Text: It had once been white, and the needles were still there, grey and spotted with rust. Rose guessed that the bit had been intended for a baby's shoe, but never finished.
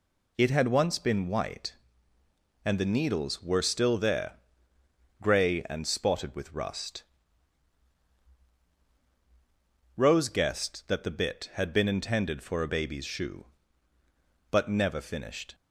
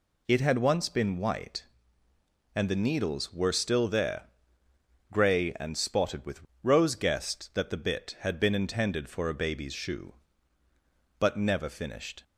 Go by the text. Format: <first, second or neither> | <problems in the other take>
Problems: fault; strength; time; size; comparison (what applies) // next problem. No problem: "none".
first | skips "rust"; at 6.5 s